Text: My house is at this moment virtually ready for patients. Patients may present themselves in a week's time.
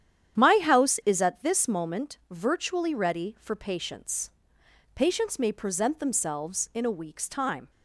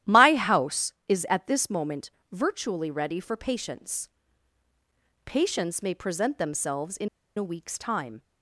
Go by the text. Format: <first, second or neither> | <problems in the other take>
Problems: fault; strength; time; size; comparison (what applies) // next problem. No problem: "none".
first | starts louder than the rest; strong; until 1.2 s; 12.5 dB; strong in the first // pauses between "moment" and "virtually"; slight; at 2.1 s; 0.18 s long // pauses between "in" and "a"; slight; at 7.0 s; 0.28 s long